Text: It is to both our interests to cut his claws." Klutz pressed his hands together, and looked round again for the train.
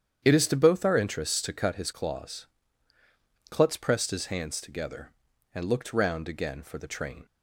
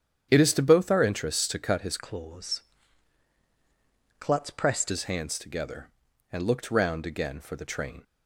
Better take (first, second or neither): first